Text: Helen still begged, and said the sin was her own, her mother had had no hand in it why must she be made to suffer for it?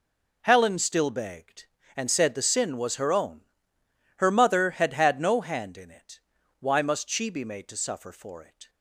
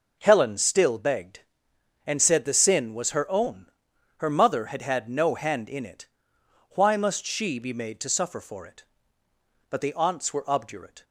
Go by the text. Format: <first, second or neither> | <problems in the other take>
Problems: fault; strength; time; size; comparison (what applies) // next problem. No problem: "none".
first | pauses between "it" and "why"; noticeable; at 6.0 s; 0.64 s long; also in the first // goes on to say "But the aunts were obdurate"; from 9.6 s on; 1.3 s long